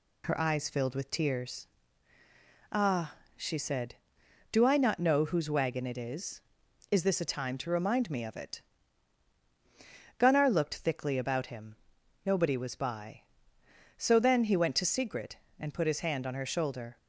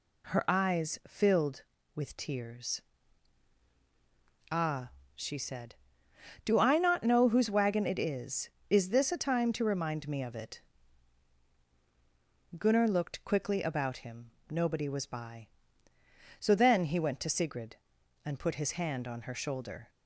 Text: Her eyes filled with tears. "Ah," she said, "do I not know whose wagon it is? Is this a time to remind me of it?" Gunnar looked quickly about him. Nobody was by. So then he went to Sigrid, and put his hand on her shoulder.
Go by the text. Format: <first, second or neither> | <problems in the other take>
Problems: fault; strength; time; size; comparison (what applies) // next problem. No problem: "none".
second | says "thickly" for "quickly"; at 10.7 s